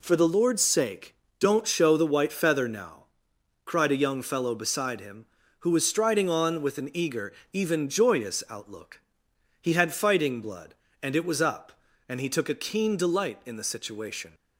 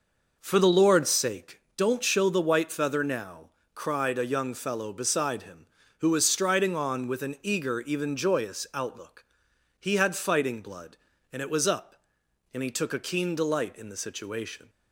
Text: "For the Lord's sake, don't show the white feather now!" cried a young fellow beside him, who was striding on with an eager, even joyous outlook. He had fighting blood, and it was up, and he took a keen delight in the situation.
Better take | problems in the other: neither | none

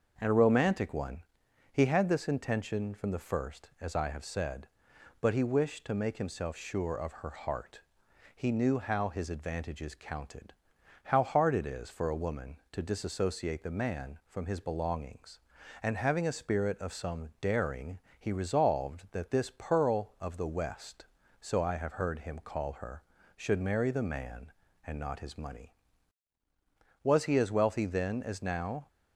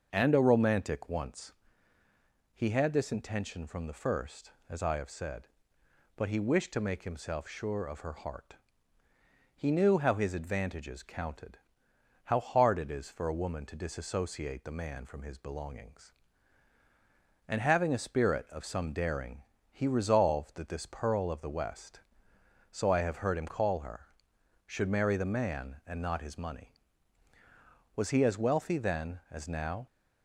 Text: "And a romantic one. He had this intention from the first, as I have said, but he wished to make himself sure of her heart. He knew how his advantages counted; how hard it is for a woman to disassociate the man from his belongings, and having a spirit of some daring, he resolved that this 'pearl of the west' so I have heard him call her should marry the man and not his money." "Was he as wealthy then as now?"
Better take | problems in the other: first | starts louder than the rest; until 1.1 s; 6 dB; also in the first // says "once" for "one"; at 1.0 s

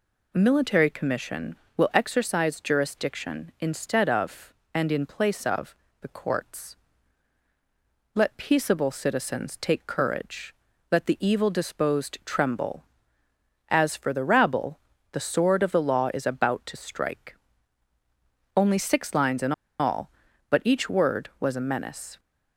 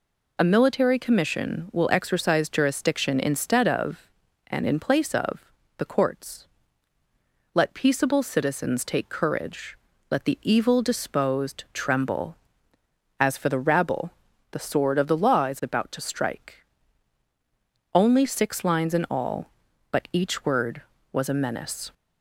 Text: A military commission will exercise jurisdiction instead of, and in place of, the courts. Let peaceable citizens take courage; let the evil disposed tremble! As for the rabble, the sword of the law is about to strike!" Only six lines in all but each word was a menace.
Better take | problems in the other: second | pauses between "in" and "all"; slight; at 19.5 s; 0.25 s long

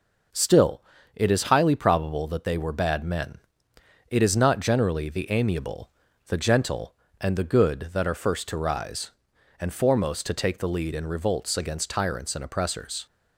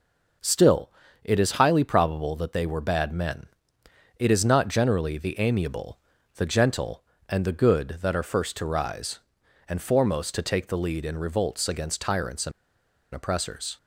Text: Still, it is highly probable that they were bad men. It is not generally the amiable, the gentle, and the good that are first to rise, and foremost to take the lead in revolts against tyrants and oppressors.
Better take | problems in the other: first | pauses between "and" and "oppressors"; noticeable; at 12.5 s; 0.63 s long

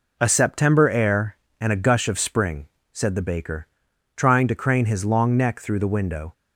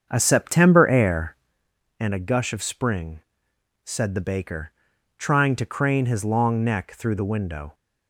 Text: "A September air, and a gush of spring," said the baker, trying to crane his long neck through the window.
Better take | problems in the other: first | starts louder than the rest; strong; until 1.7 s; 7 dB

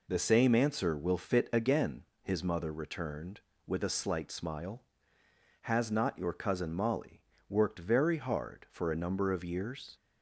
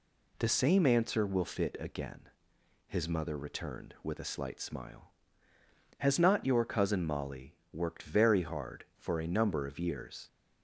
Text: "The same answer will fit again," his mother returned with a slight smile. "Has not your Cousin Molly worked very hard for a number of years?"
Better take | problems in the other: neither | pauses between "Molly" and "worked"; slight; the same in both

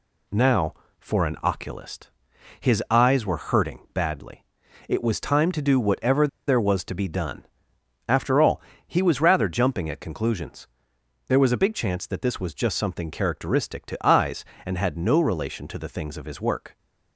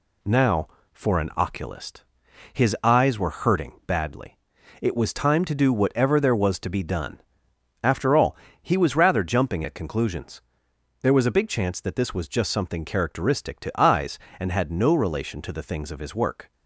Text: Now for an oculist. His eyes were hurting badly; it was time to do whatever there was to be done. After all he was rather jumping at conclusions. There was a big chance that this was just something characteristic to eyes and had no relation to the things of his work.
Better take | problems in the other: second | pauses between "whatever" and "there"; slight; at 6.2 s; 0.20 s long // pauses between "all" and "he"; slight; at 8.6 s; 0.24 s long; slight in the second

